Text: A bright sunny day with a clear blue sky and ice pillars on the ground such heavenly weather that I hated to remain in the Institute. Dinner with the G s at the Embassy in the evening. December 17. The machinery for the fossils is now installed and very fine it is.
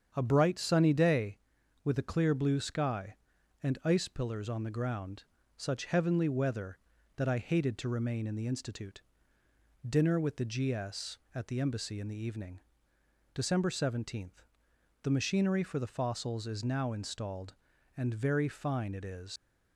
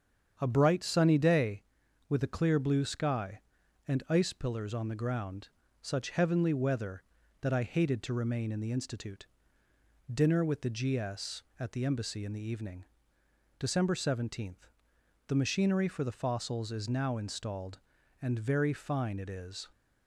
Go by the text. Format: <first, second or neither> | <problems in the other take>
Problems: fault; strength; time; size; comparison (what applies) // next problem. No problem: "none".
second | starts louder than the rest; strong; until 1.1 s; 8 dB; strong in the second // pauses between "ground" and "such"; slight; at 5.2 s; 0.32 s long; slight in the second // leaves "is" unfinished; at 19.3 s; 100 ms